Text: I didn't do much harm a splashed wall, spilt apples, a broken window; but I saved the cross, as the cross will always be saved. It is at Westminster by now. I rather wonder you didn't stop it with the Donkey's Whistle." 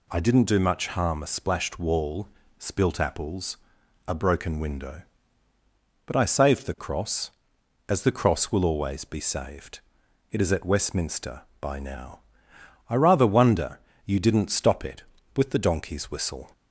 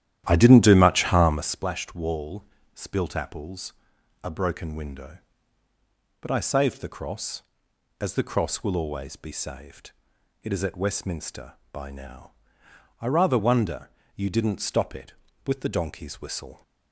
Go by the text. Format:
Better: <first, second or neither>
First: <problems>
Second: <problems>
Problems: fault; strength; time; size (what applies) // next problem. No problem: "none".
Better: first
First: pauses between "wonder" and "you"; slight; at 13.8 s; 0.24 s long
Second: starts louder than the rest; strong; until 1.7 s; 12 dB // pauses between "wonder" and "you"; slight; at 13.9 s; 0.24 s long